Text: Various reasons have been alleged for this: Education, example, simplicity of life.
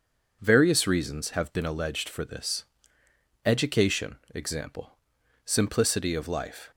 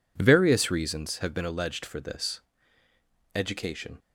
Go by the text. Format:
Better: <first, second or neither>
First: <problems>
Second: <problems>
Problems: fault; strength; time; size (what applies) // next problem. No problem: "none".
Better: first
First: none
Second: stops before "example simplicity of life"; at 3.9 s